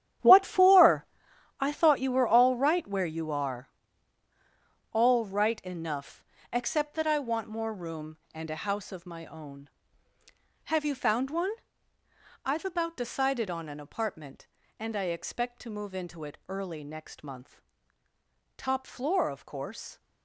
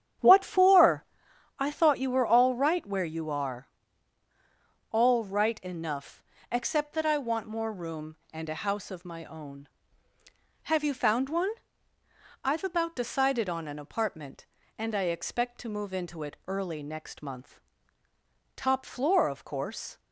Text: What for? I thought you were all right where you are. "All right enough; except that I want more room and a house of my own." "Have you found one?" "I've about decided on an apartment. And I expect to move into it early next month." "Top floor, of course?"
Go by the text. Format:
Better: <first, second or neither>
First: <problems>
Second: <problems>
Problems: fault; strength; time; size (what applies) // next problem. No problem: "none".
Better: second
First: gets quieter; strong; throughout; 12.5 dB // starts louder than the rest; strong; until 1.7 s; 10.5 dB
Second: starts louder than the rest; strong; until 1.7 s; 9 dB